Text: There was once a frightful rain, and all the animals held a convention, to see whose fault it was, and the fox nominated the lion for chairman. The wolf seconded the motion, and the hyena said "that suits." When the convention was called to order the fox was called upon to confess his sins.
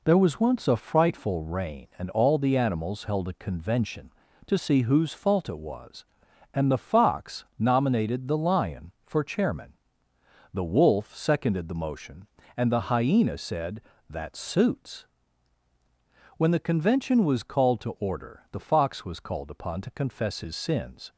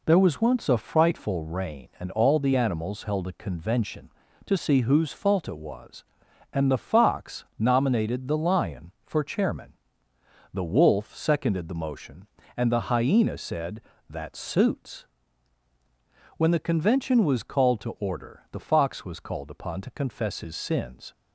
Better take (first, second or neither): neither